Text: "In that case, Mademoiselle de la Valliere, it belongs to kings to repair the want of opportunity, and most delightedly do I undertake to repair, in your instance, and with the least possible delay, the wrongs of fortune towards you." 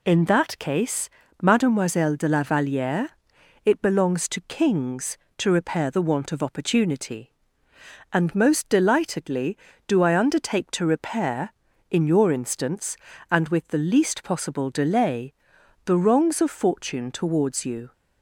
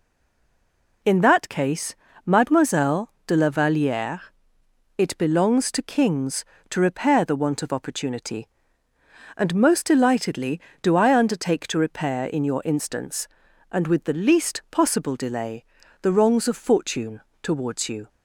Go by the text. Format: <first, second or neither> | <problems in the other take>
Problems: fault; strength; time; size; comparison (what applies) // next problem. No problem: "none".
first | stays silent before the first word; until 1.0 s; 1.0 s long // pauses between "fortune" and "towards"; slight; at 17.1 s; 0.22 s long